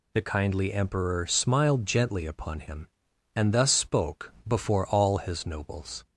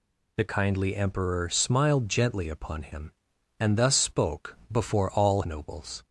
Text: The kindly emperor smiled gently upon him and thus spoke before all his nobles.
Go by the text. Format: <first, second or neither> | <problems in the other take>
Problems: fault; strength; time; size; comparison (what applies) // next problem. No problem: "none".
first | pauses between "spoke" and "before"; slight; at 4.5 s; 0.16 s long; slight in the first // skips "his"; at 5.4 s